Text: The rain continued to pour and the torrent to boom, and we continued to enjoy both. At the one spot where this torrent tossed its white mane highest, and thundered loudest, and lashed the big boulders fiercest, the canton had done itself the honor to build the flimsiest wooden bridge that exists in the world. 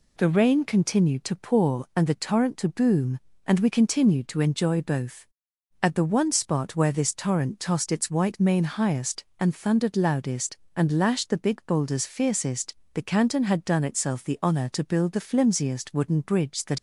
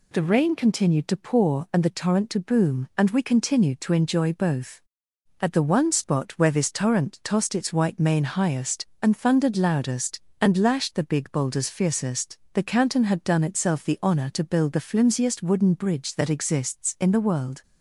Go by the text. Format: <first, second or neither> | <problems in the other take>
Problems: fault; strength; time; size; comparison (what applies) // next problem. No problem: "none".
second | stops before "exists in the world"; at 16.7 s